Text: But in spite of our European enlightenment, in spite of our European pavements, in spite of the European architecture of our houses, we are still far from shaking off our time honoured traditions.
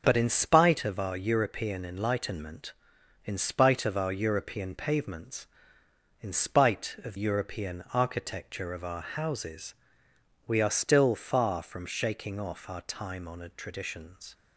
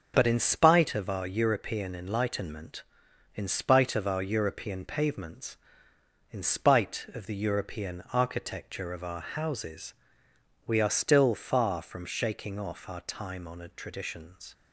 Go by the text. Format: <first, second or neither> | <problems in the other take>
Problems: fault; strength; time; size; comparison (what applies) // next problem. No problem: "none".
second | skips "the"; at 7.1 s